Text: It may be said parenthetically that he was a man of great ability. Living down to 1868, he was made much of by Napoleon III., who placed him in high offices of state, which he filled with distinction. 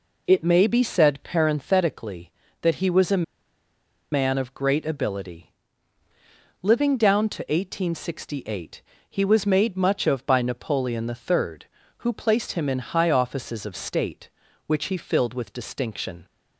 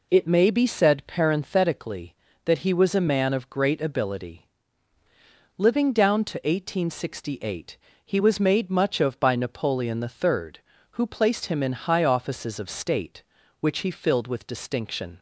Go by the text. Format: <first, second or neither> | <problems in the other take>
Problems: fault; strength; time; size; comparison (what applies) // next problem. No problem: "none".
second | pauses between "a" and "man"; noticeable; at 3.2 s; 0.88 s long